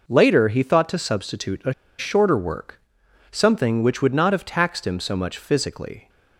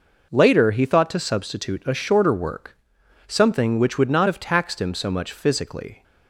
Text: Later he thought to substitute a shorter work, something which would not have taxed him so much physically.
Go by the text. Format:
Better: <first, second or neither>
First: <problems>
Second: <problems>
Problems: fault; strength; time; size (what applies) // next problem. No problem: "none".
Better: second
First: pauses between "a" and "shorter"; slight; at 1.7 s; 0.26 s long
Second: none